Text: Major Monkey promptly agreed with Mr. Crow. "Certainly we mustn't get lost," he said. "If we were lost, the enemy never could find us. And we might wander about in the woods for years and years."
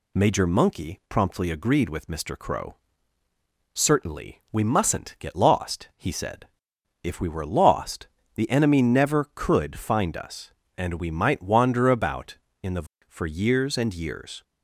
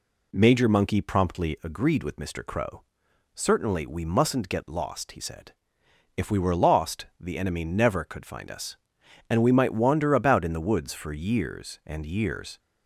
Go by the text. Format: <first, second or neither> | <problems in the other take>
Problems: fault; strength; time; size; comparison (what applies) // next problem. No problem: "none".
second | skips "woods"; at 12.9 s